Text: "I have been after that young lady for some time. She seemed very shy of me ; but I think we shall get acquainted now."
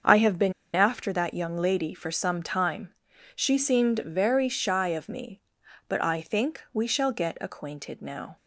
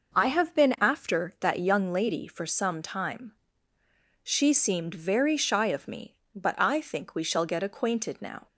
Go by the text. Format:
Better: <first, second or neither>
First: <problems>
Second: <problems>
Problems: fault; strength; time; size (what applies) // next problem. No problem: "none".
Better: second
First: starts louder than the rest; until 1.2 s; 6.5 dB // pauses between "been" and "after"; slight; at 0.5 s; 0.23 s long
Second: none